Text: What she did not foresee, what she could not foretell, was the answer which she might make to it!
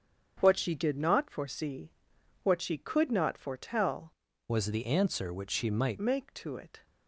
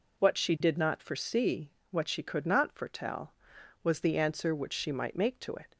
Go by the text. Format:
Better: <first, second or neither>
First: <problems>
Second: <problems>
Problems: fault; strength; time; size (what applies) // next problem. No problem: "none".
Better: second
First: starts louder than the rest; strong; until 1.4 s; 7.5 dB // changes voice from "was" to "might"; from 4.4 to 5.9 s; 1.5 s long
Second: none